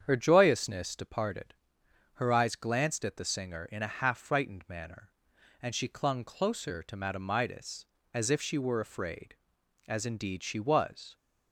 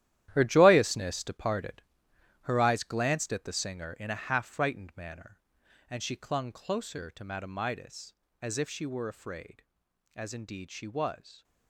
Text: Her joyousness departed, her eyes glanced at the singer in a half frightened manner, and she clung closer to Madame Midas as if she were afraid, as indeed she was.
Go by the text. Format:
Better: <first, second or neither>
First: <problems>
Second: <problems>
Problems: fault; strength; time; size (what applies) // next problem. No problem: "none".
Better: first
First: starts louder than the rest; strong; until 1.0 s; 8 dB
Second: gets quieter; strong; throughout; 11.5 dB // starts louder than the rest; strong; until 1.3 s; 12.5 dB